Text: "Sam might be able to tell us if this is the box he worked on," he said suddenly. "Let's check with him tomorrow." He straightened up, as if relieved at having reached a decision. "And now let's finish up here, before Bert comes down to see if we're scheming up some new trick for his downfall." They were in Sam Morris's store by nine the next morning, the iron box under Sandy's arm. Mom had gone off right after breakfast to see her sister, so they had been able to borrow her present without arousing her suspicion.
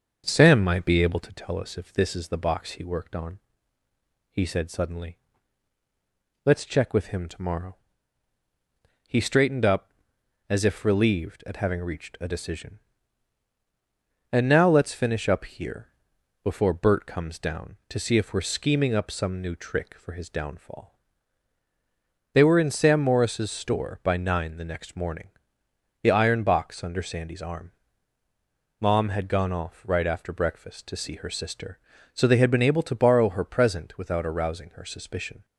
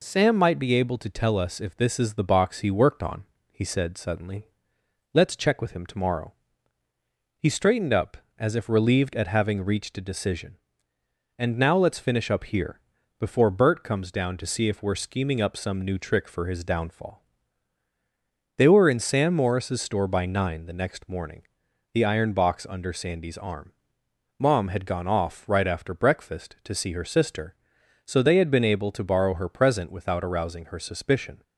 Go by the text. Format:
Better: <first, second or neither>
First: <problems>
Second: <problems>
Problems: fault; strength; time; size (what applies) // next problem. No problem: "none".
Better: second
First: starts louder than the rest; until 1.4 s; 6.5 dB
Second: none